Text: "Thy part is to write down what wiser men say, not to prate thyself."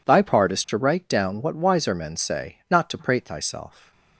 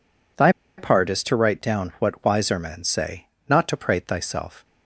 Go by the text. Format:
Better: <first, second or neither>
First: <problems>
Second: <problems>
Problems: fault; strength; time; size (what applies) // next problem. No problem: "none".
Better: first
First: none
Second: pauses between "Thy" and "part"; slight; at 0.5 s; 0.26 s long